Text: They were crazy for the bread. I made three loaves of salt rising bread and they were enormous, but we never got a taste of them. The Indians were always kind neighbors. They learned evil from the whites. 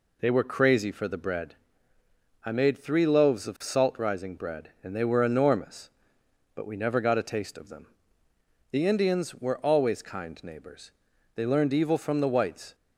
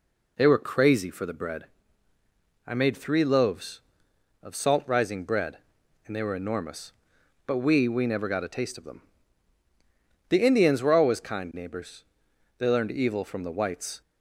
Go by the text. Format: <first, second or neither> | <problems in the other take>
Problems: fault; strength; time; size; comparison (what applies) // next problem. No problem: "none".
first | says "we" twice; at 7.8 s